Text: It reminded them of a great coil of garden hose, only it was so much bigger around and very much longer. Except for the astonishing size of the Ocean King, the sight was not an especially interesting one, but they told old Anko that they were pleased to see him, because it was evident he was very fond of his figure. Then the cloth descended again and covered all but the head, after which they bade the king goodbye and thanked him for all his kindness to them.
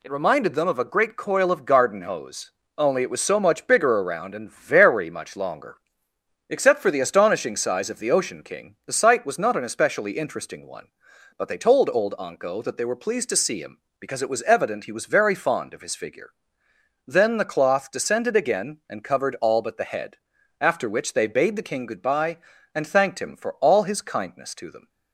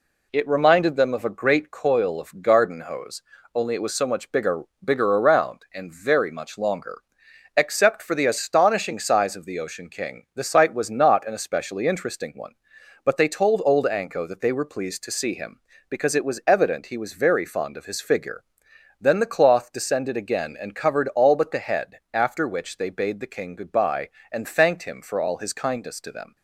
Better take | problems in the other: first | says "bigger" twice; at 4.8 s

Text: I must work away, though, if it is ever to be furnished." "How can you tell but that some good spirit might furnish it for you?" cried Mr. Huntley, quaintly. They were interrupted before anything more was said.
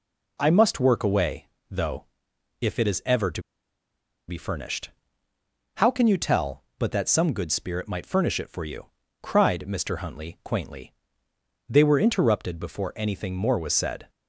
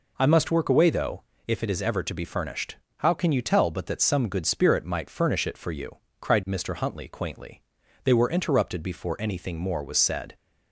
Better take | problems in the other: second | pauses between "to" and "be"; noticeable; at 3.4 s; 0.86 s long

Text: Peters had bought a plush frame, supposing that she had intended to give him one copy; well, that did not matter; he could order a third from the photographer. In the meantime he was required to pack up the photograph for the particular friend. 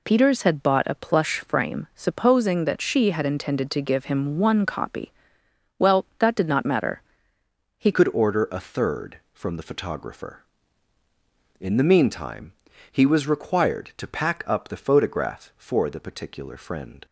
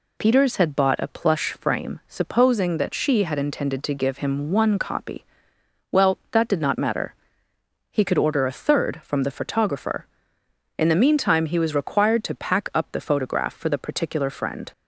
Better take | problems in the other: second | changes voice at "could"; from 7.9 s on; 9.1 s long // pauses between "meantime" and "he"; at 12.5 s; 0.40 s long

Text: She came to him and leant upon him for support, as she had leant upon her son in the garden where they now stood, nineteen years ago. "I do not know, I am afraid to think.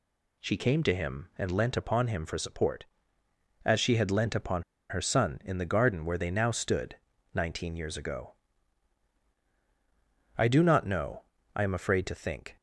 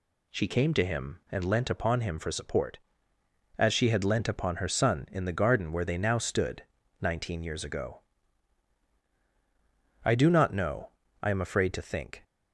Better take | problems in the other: second | pauses between "upon" and "her"; slight; at 4.6 s; 0.26 s long

